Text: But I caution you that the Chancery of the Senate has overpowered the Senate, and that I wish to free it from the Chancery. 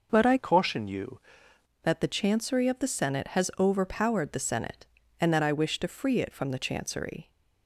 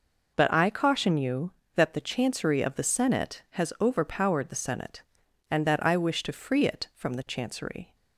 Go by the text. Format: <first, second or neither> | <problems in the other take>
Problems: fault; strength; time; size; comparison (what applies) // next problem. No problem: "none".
second | changes voice from "caution" to "you"; from 0.3 to 1.1 s; 0.8 s long